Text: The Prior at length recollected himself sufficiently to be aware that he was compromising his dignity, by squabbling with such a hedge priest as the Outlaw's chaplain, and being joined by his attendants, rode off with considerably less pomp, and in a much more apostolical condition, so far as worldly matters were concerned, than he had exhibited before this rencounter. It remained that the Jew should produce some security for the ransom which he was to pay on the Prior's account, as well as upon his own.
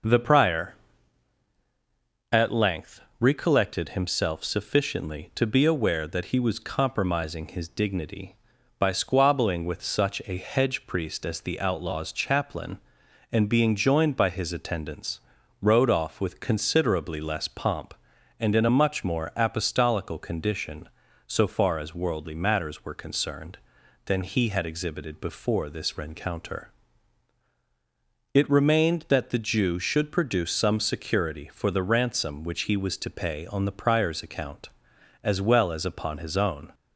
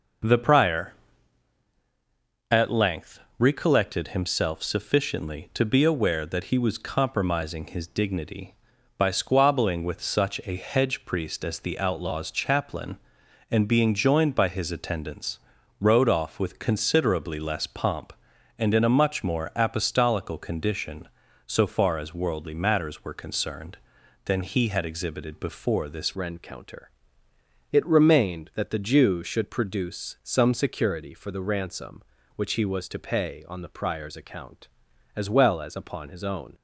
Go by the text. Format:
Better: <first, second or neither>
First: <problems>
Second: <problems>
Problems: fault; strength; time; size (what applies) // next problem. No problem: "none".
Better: first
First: pauses between "length" and "recollected"; slight; at 3.0 s; 0.18 s long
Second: pauses between "length" and "recollected"; slight; at 3.1 s; 0.18 s long // changes voice at "rencounter"; from 26.1 s on; 10.4 s long